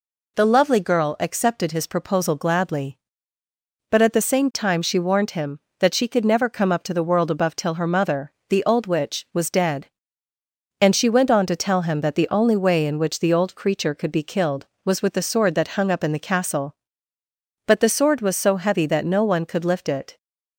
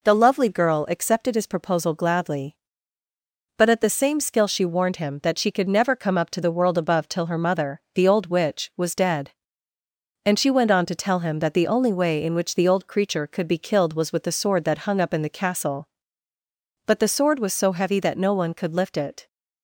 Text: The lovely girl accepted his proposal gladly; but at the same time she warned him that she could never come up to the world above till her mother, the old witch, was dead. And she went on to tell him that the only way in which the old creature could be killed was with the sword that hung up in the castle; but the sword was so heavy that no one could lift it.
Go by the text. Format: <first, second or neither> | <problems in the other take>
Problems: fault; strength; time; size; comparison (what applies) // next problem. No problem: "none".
first | says "skill" for "time"; at 4.1 s